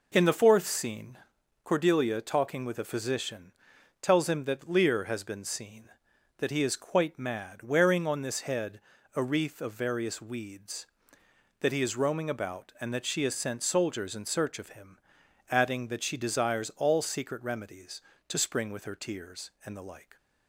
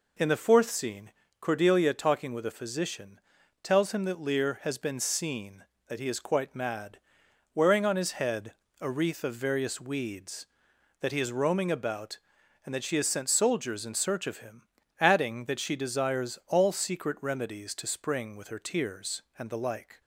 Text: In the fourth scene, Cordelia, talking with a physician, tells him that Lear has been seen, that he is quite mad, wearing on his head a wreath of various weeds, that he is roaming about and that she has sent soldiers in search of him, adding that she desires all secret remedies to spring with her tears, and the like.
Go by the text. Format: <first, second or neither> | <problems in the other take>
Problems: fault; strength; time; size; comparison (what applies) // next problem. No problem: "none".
second | says "this" for "his"; at 8.2 s // pauses between "head" and "a"; slight; at 8.7 s; 0.36 s long; slight in the second